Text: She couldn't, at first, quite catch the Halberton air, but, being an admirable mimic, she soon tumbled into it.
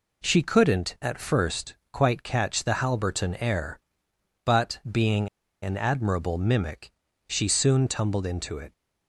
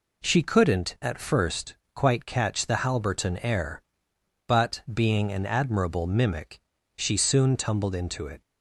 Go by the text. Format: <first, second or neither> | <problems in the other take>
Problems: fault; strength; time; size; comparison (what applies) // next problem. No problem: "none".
second | pauses between "being" and "an"; slight; at 5.2 s; 0.33 s long